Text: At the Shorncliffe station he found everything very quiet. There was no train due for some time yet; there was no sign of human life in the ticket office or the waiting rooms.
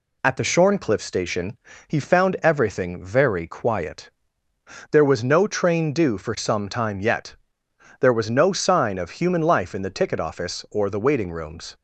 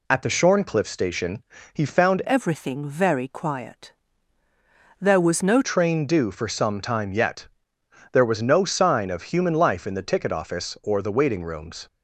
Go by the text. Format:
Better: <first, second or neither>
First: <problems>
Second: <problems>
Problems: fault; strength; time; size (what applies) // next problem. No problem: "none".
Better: first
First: pauses between "station" and "he"; slight; at 1.5 s; 0.32 s long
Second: pauses between "station" and "he"; slight; at 1.4 s; 0.32 s long // changes voice from "everything" to "no"; from 2.2 to 5.6 s; 3.4 s long